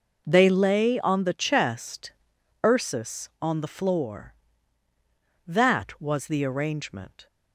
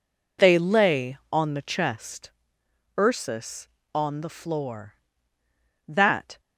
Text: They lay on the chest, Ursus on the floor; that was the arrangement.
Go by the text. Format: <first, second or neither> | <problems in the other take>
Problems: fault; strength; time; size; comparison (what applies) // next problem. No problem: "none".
first | stops before "was the arrangement"; at 6.3 s